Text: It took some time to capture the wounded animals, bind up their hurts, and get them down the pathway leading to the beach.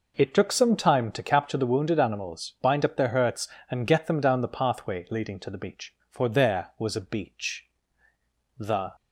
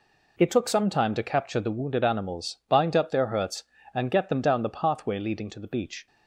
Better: second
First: goes on to say "For there was a beach the"; strong; from 6.0 s on; 2.8 s long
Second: none

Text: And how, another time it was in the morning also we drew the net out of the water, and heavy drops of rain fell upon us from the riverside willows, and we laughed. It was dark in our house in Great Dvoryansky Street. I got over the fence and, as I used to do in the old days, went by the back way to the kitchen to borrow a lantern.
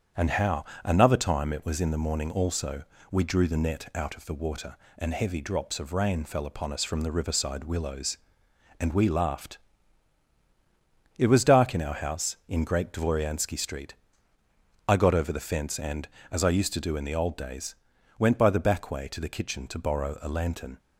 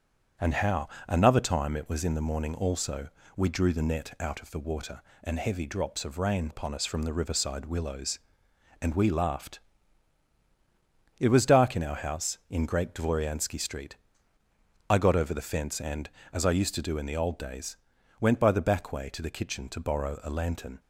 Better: first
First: starts louder than the rest; strong; until 1.3 s; 8 dB // pauses between "also" and "we"; slight; at 2.8 s; 0.26 s long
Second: starts louder than the rest; until 1.6 s; 7 dB // pauses between "also" and "we"; slight; at 3.0 s; 0.26 s long // skips "fell"; at 6.4 s

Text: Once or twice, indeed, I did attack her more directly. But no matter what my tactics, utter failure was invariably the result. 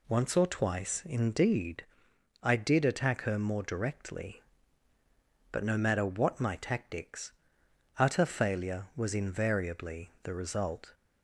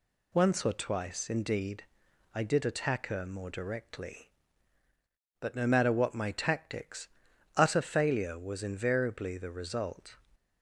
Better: neither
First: none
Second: none

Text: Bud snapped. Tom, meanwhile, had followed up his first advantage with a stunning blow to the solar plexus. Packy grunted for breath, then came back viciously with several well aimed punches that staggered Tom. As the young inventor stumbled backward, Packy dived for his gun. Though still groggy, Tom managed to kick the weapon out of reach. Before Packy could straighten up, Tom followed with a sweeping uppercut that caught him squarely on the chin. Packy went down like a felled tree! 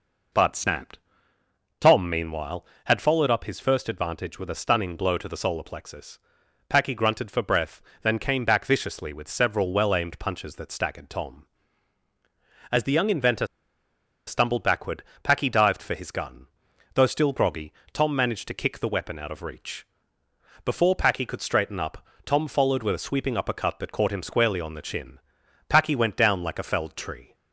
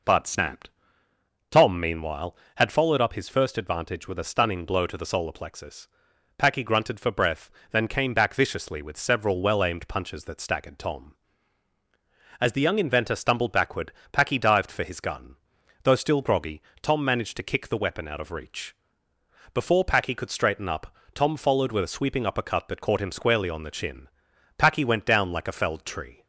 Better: second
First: pauses between "inventor" and "stumbled"; noticeable; at 13.4 s; 0.80 s long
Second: none

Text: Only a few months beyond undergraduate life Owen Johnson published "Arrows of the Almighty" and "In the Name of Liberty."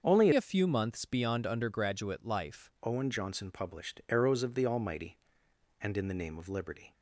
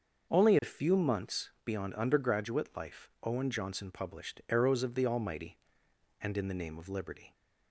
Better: second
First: starts louder than the rest; until 1.0 s; 6.5 dB // changes voice from "a" to "life"; from 0.3 to 2.7 s; 2.4 s long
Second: starts louder than the rest; until 1.3 s; 6.5 dB

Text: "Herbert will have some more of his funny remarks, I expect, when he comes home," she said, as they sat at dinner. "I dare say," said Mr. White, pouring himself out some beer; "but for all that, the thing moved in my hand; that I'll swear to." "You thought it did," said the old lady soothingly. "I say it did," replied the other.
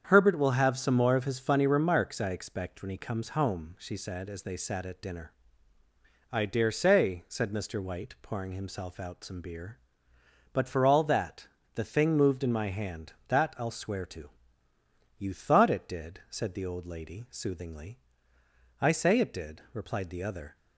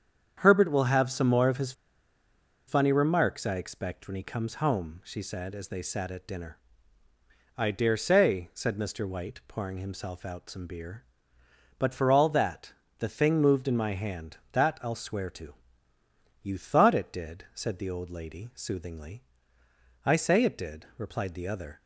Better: first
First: starts louder than the rest; strong; until 1.1 s; 8 dB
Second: starts louder than the rest; strong; until 1.4 s; 8 dB // pauses between "his" and "funny"; noticeable; at 1.7 s; 0.95 s long

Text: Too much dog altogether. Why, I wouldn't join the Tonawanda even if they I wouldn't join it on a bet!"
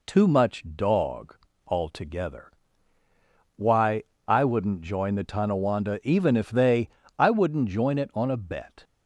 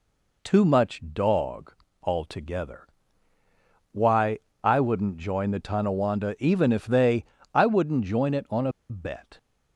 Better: first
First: pauses between "dog" and "altogether"; slight; at 1.3 s; 0.29 s long // pauses between "they" and "I"; slight; at 6.8 s; 0.28 s long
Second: pauses between "dog" and "altogether"; slight; at 1.7 s; 0.28 s long // pauses between "they" and "I"; slight; at 7.2 s; 0.28 s long // pauses between "a" and "bet"; slight; at 8.7 s; 0.18 s long

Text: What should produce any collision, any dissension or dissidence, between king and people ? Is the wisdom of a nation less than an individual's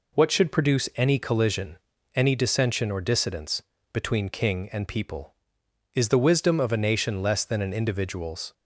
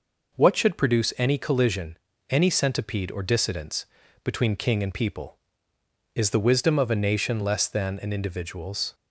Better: first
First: none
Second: says "centipede" for "dissension"; at 2.4 s

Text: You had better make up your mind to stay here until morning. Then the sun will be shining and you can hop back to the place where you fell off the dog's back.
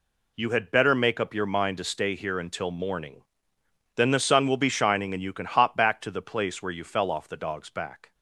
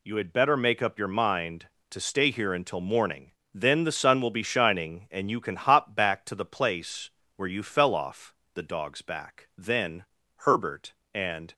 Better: first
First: none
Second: pauses between "place" and "where"; slight; at 7.0 s; 0.26 s long // pauses between "off" and "the"; slight; at 8.3 s; 0.22 s long // goes on to say "Then Herbert and"; strong; from 9.5 s on; 1.9 s long

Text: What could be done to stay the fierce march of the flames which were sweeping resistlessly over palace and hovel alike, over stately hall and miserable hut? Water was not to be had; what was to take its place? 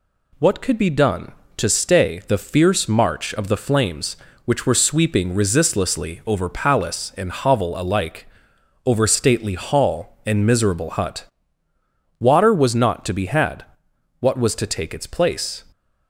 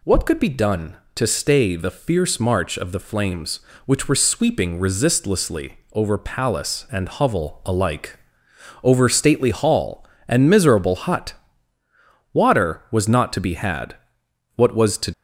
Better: first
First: none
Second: pauses between "resistlessly" and "over"; slight; at 5.7 s; 0.15 s long // stops before "take its place"; at 15.1 s

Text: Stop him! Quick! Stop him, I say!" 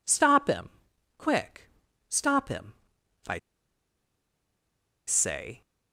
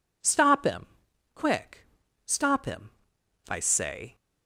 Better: second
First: pauses between "I" and "say"; strong; at 3.3 s; 1.6 s long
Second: none

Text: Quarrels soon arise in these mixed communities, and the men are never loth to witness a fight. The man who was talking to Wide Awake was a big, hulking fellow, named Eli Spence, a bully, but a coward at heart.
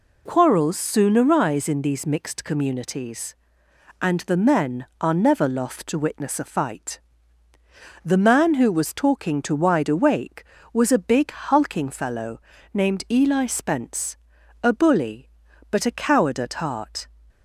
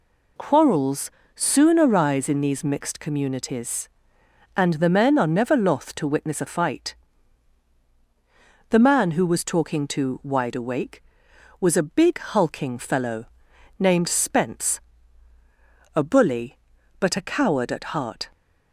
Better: first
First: none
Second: pauses between "Quarrels" and "soon"; slight; at 1.0 s; 0.26 s long // skips "Eli"; at 14.0 s

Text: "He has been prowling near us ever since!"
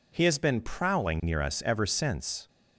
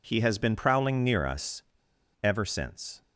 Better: first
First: none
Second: pauses between "us" and "ever"; noticeable; at 1.6 s; 0.60 s long

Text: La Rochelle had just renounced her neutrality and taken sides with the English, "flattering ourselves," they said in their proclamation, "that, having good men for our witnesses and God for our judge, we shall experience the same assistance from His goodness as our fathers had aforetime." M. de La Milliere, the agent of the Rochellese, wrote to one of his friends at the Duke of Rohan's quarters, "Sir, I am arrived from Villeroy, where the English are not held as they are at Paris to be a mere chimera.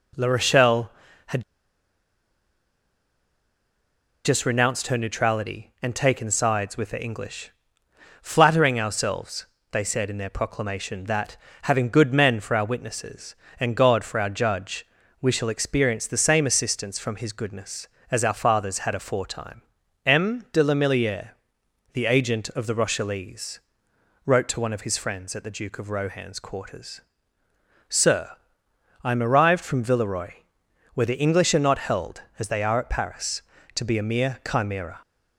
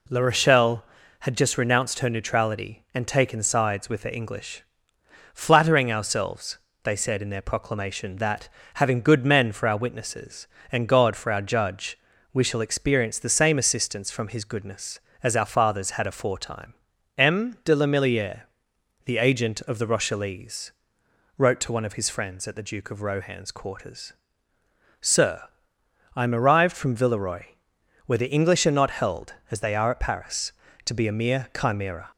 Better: second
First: pauses between "had" and "just"; strong; at 1.4 s; 2.8 s long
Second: none

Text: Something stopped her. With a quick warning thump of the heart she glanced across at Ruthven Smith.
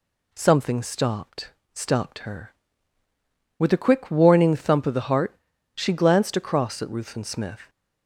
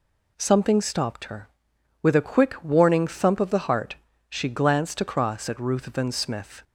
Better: second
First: says "stopped" twice; at 1.7 s // pauses between "heart" and "she"; at 5.3 s; 0.40 s long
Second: pauses between "heart" and "she"; slight; at 3.9 s; 0.34 s long

